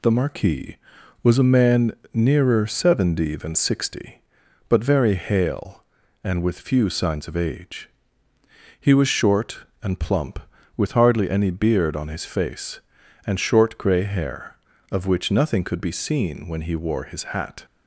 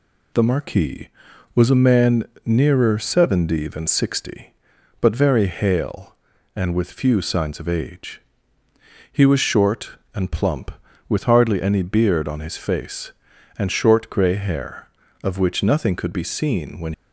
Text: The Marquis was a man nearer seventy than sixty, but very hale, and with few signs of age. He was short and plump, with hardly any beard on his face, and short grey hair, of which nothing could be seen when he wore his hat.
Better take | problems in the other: first | pauses between "man" and "nearer"; slight; at 2.2 s; 0.20 s long; slight in the first // stops before "he wore his hat"; at 16.9 s

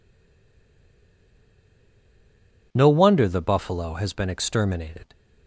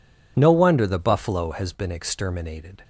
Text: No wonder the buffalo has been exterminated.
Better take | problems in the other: second | stays silent before the first word; strong; until 2.7 s; 2.7 s long

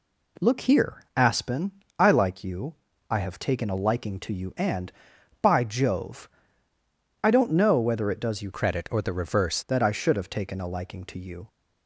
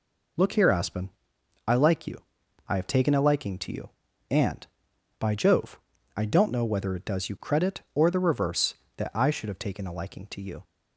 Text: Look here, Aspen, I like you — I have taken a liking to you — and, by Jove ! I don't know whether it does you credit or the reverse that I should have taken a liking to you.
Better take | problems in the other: second | changes voice from "credit" to "reverse"; from 8.5 to 9.6 s; 1.1 s long

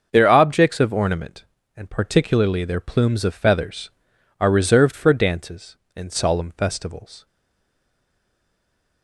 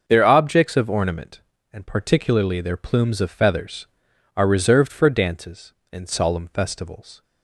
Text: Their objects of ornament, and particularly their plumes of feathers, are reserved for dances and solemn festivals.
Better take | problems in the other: second | stays silent after the last word; noticeable; from 7.2 s on; 1.8 s long

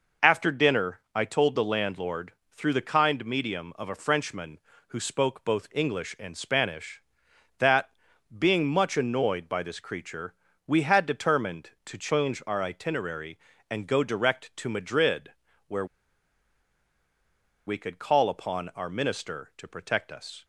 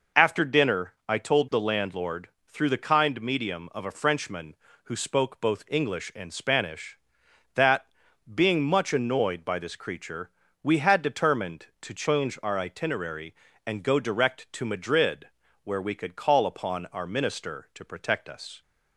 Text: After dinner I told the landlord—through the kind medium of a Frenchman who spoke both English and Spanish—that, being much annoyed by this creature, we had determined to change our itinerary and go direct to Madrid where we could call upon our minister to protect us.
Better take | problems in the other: second | pauses between "dinner" and "I"; slight; at 0.9 s; 0.16 s long; slight in the second // pauses between "Madrid" and "where"; at 15.2 s; 0.38 s long; also in the second // pauses between "where" and "we"; strong; at 15.8 s; 1.8 s long

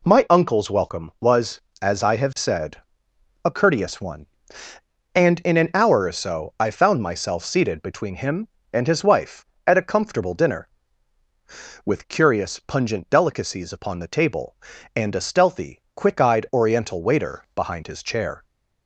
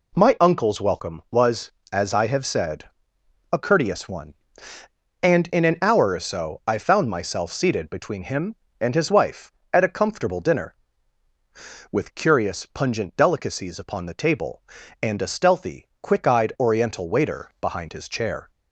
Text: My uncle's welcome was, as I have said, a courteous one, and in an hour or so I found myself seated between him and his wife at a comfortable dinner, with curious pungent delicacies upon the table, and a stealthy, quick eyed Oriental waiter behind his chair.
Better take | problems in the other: neither | none

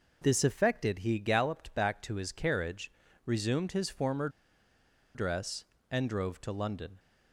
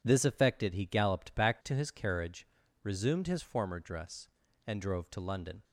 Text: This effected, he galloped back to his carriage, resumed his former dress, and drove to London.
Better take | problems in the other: second | pauses between "former" and "dress"; noticeable; at 4.2 s; 0.86 s long

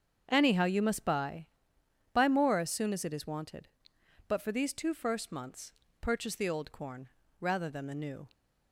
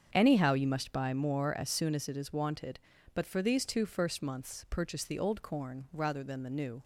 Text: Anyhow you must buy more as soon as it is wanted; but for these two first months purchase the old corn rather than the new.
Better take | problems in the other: second | starts louder than the rest; strong; until 1.2 s; 7 dB; strong in the second // says "buy" twice; at 2.1 s // pauses between "months" and "purchase"; slight; at 5.7 s; 0.28 s long // pauses between "corn" and "rather"; slight; at 7.0 s; 0.32 s long

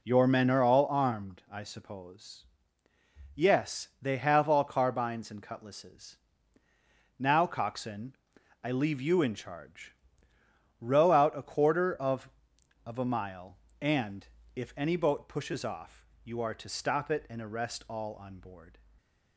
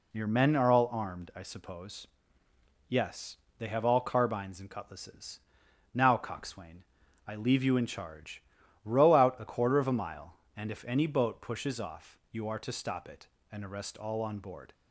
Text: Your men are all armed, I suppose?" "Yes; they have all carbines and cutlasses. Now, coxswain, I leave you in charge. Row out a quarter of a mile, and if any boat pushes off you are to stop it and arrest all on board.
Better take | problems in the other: second | says "of" twice; at 12.8 s // pauses between "and" and "if"; slight; at 14.2 s; 0.28 s long // pauses between "off" and "you"; slight; at 16.0 s; 0.18 s long

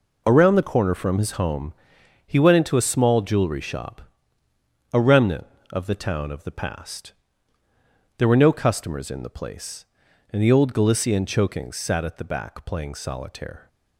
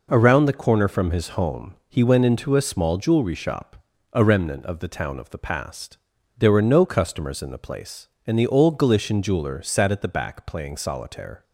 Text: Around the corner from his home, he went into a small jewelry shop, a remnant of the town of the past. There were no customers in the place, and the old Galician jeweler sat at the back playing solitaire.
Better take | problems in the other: second | says "chokings" for "jeweler"; at 11.2 s

